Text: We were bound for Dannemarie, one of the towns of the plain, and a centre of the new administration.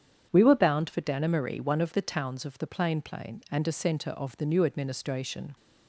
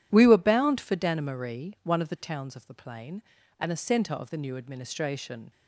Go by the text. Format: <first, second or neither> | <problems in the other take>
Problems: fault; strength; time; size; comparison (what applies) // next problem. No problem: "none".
second | starts louder than the rest; strong; until 1.3 s; 8.5 dB // says "plain" twice; at 3.0 s